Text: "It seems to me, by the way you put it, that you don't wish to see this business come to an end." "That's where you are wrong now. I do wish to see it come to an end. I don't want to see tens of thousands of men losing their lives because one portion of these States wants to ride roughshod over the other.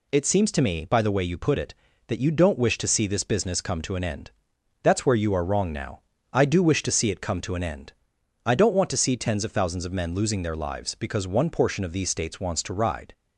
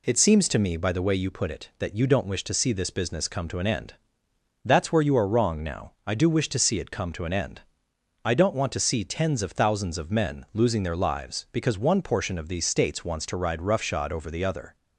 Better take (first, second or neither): second